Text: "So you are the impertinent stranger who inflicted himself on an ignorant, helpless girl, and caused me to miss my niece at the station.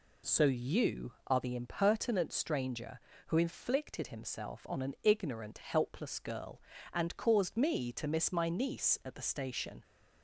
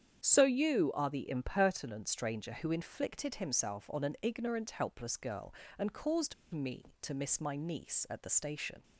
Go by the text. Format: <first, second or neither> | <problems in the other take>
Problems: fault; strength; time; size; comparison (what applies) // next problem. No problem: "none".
first | starts louder than the rest; strong; until 1.2 s; 8.5 dB // pauses between "caused" and "me"; slight; at 6.3 s; 0.18 s long